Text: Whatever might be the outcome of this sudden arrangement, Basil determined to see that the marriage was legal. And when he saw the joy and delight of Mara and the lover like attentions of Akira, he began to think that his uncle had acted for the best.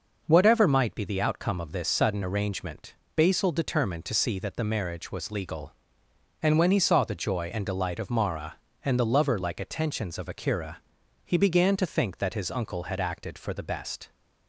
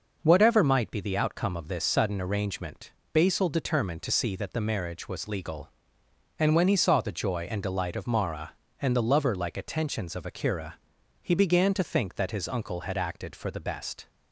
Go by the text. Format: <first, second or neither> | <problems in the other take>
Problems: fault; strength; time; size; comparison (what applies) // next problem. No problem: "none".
neither | none